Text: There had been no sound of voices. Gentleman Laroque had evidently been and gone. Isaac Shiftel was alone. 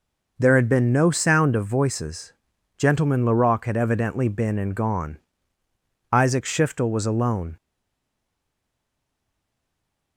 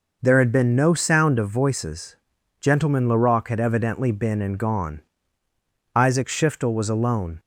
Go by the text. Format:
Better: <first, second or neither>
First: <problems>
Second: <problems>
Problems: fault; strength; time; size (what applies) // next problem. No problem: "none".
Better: second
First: stays silent after the last word; strong; from 7.5 s on; 2.6 s long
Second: none